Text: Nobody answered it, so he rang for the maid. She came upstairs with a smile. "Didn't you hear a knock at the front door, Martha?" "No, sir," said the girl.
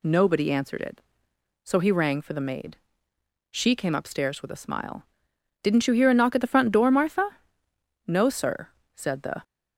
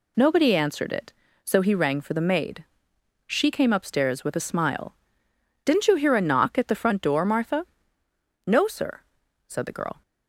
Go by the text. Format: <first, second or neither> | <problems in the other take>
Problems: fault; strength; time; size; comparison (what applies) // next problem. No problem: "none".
second | stops before "girl"; at 9.4 s